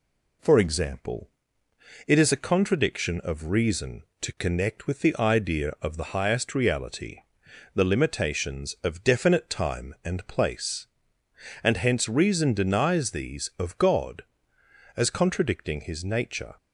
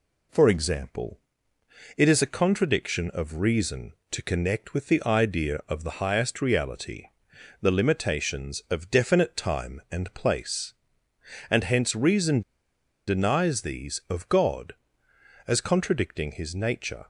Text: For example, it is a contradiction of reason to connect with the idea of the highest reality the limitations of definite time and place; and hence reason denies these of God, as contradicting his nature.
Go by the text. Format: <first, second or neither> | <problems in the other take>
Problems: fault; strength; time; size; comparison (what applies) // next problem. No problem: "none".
first | pauses between "reality" and "the"; noticeable; at 7.0 s; 0.54 s long; noticeable in the first // pauses between "reason" and "denies"; noticeable; at 12.4 s; 0.66 s long